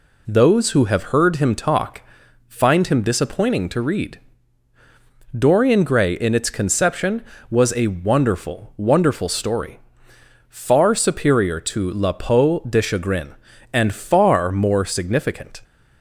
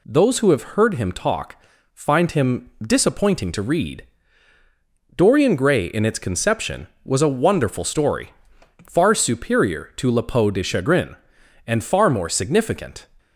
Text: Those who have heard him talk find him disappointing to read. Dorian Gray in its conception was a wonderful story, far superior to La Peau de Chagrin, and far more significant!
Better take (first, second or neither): second